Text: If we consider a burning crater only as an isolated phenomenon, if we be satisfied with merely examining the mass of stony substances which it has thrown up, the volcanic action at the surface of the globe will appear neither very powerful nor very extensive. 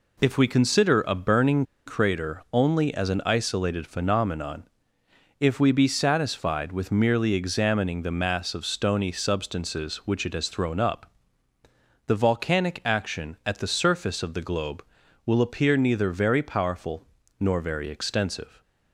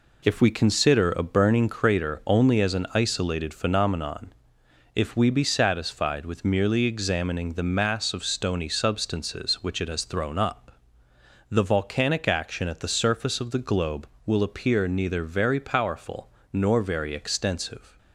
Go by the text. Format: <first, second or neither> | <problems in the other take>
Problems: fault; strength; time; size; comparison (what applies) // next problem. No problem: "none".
second | pauses between "burning" and "crater"; slight; at 1.6 s; 0.23 s long // pauses between "powerful" and "nor"; slight; at 17.0 s; 0.34 s long; slight in the second